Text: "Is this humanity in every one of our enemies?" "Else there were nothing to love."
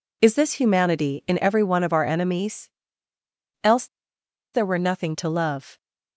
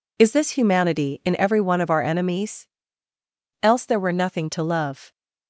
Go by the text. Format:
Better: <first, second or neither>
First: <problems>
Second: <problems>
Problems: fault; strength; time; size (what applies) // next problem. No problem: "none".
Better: second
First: pauses between "Else" and "there"; noticeable; at 3.8 s; 0.67 s long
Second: none